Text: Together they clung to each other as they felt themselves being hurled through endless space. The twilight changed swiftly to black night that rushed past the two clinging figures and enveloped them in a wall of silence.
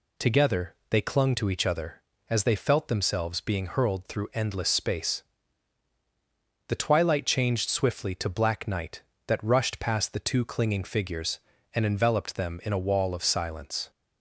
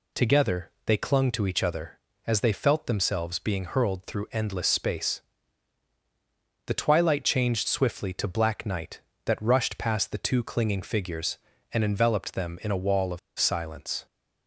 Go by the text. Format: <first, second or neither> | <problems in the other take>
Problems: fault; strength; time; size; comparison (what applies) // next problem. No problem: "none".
first | pauses between "of" and "silence"; slight; at 13.1 s; 0.20 s long